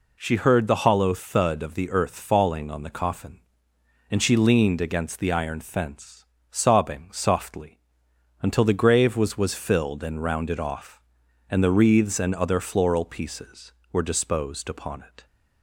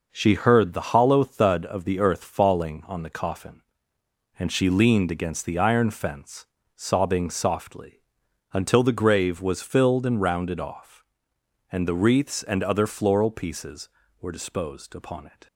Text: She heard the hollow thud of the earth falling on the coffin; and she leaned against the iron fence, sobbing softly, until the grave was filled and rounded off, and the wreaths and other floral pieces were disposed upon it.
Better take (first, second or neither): second